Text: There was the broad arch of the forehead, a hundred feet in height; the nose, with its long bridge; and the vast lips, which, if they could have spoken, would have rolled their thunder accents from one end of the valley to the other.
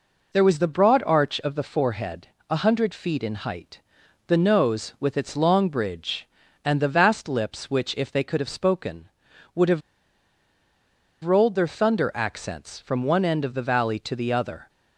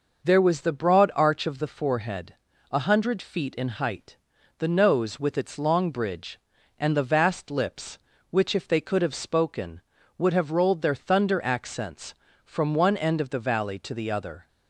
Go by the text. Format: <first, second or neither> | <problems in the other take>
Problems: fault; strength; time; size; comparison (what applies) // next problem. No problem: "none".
second | pauses between "have" and "rolled"; strong; at 9.8 s; 1.4 s long